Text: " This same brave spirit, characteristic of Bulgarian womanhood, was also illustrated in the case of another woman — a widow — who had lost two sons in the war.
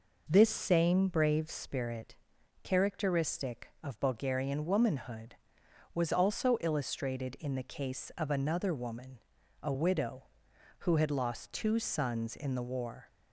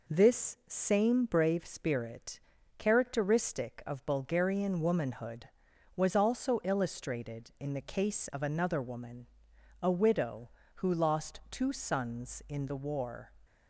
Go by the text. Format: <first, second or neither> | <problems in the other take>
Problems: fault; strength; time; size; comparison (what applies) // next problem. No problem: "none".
first | skips "had"; at 10.9 s